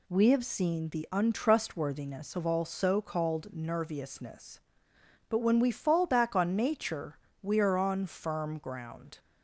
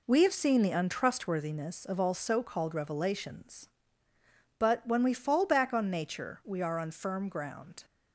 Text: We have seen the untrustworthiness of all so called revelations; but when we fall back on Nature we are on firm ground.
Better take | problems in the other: second | says "nerviousness" for "revelations"; at 3.5 s // pauses between "Nature" and "we"; slight; at 7.1 s; 0.24 s long

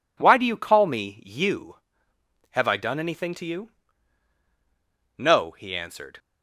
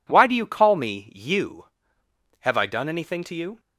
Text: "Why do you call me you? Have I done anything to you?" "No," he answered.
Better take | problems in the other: first | stops before "No he answered"; at 3.5 s

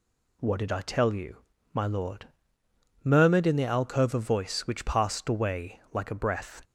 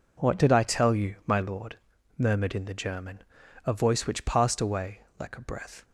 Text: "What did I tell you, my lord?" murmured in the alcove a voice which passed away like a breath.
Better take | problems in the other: first | says "german" for "alcove"; at 2.7 s // pauses between "away" and "like"; slight; at 5.0 s; 0.18 s long

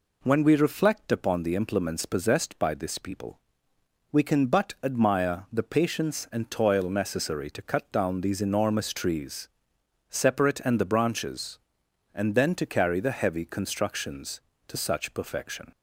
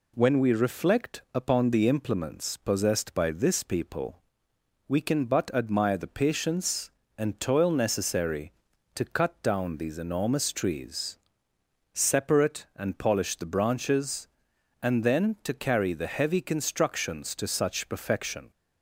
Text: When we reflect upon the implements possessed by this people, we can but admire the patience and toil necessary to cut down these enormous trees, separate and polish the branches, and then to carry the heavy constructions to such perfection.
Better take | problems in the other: second | skips "polish"; at 10.7 s

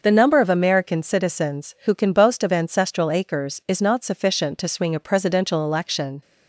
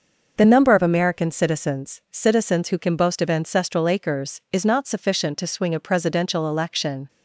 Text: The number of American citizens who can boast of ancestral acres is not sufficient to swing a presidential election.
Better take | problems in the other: first | starts louder than the rest; noticeable; until 1.3 s; 6 dB; also in the first // says "citizens" twice; at 2.0 s

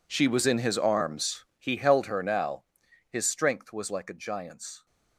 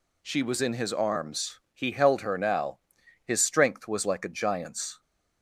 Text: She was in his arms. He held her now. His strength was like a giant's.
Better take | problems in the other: second | gets quieter; strong; throughout; 18 dB

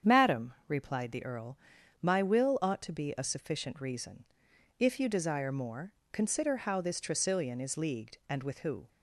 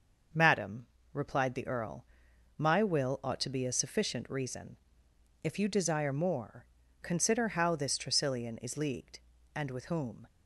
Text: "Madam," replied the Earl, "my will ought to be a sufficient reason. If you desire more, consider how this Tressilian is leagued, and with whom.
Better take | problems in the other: second | starts louder than the rest; strong; until 1.2 s; 8 dB; also in the second // says "who" for "whom"; at 8.5 s

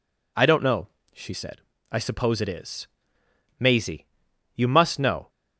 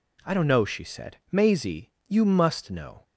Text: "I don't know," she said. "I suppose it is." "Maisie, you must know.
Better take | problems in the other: first | skips "I suppose it is"; at 1.2 s

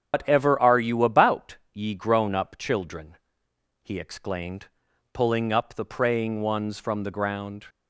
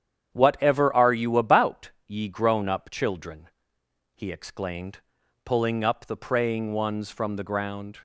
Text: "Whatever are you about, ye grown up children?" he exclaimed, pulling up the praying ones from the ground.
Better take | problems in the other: second | loses the start of "Whatever"; at 0.1 s; 135 ms // starts louder than the rest; strong; until 1.1 s; 7.5 dB; strong in the second

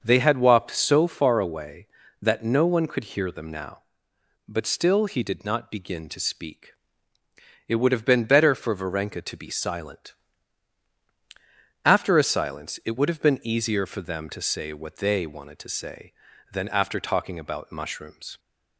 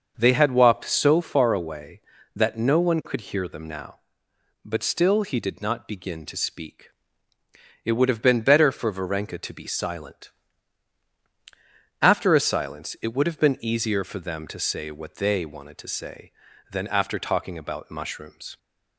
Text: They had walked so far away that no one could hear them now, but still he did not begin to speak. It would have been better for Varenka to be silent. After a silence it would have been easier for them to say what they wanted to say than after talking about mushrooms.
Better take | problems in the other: neither | starts louder than the rest; the same in both

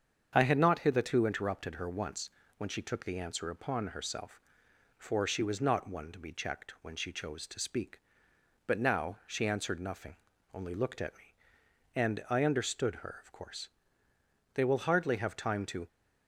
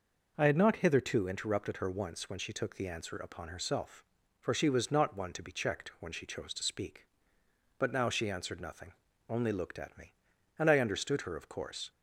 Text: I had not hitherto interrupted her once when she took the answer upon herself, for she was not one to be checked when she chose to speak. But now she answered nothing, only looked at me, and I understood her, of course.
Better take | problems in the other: second | starts louder than the rest; strong; until 1.3 s; 7.5 dB // pauses between "once" and "when"; slight; at 2.2 s; 0.30 s long // goes on to say "They will hardly have time to"; from 14.5 s on; 1.3 s long

